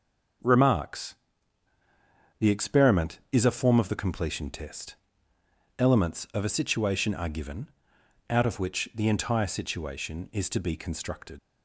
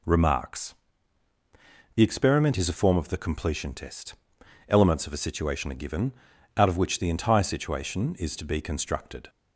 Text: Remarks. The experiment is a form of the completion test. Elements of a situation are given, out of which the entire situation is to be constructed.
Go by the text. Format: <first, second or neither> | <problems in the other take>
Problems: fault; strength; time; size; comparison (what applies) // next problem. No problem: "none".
second | leaves "constructed" unfinished; at 11.3 s; 70 ms